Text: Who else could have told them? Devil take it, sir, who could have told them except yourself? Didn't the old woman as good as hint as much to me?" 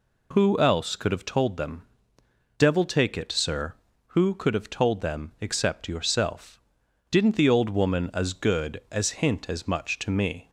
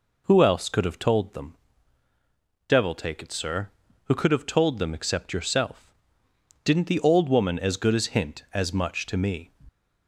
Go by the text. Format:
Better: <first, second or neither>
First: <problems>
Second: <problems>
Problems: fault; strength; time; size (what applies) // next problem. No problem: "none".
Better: neither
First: none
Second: none